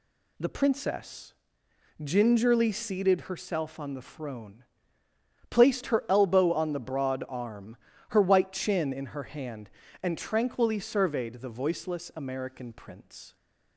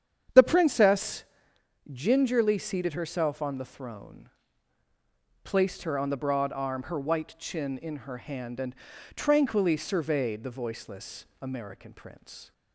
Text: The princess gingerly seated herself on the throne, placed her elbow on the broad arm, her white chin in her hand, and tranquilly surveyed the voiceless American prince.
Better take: first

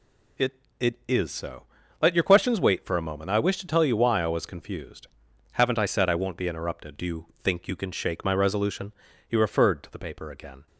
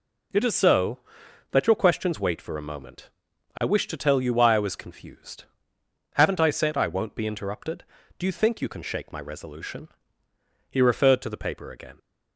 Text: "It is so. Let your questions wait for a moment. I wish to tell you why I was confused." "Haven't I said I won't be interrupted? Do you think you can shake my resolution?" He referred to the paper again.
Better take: second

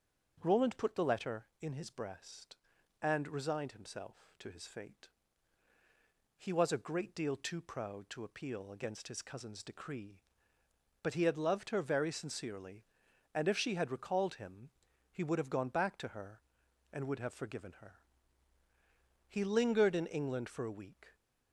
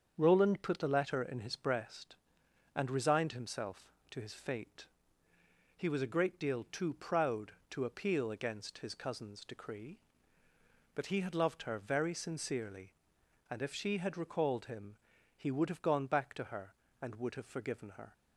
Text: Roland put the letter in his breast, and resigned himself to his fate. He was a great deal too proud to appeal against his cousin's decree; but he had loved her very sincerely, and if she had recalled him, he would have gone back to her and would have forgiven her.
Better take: second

